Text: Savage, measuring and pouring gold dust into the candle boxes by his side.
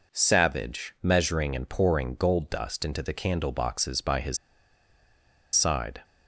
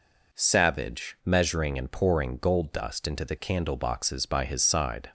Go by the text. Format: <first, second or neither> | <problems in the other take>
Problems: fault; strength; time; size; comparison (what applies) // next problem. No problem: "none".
second | pauses between "his" and "side"; at 4.3 s; 1.1 s long